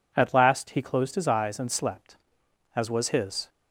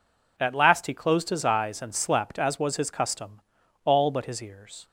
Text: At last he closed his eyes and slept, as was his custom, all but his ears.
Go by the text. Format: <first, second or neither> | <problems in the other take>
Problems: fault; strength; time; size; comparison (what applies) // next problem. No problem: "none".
second | stops before "custom all but his ears"; at 3.4 s